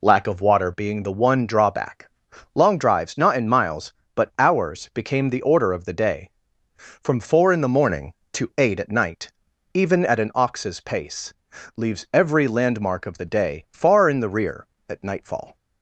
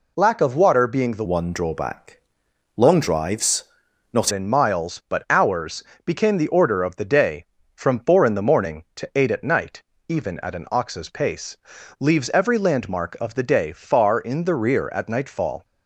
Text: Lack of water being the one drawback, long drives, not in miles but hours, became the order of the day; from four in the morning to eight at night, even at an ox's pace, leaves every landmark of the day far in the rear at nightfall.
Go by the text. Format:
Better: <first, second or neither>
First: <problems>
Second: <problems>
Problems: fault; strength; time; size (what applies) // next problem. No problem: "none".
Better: first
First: none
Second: changes voice from "one" to "not"; from 1.2 to 4.3 s; 3.1 s long